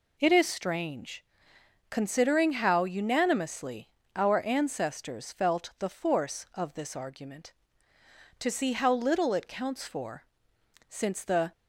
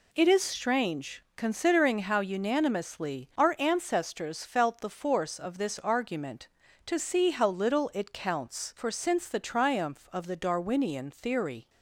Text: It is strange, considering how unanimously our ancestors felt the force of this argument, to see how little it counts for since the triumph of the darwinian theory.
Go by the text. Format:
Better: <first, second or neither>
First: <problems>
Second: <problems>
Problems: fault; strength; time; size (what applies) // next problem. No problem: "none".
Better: second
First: pauses between "unanimously" and "our"; slight; at 3.8 s; 0.26 s long // pauses between "for" and "since"; noticeable; at 10.2 s; 0.66 s long // stops before "triumph of the darwinian theory"; at 11.5 s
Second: none